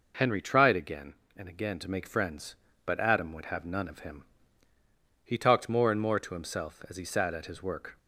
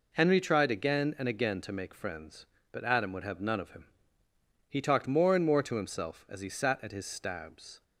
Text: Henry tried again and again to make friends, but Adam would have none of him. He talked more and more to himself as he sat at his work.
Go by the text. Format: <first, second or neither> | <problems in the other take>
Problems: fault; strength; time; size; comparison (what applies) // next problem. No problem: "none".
first | says "stabs" for "work"; at 7.0 s